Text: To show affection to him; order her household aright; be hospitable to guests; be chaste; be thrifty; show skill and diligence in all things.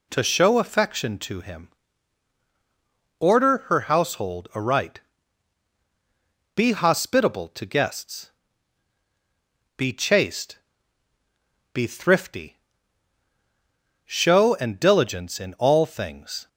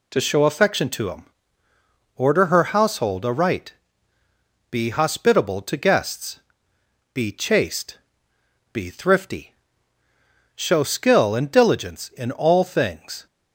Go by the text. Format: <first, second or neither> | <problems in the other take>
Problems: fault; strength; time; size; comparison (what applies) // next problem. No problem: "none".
second | skips "skill"; at 14.5 s